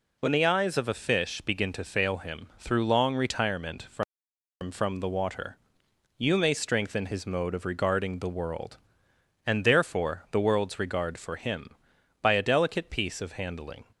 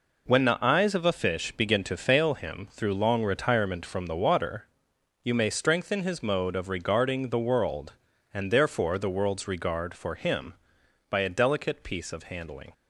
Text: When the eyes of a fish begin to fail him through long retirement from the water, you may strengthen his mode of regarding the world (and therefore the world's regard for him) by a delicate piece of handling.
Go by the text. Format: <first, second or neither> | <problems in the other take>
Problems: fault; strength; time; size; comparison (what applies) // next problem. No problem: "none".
second | says "from" twice; at 4.7 s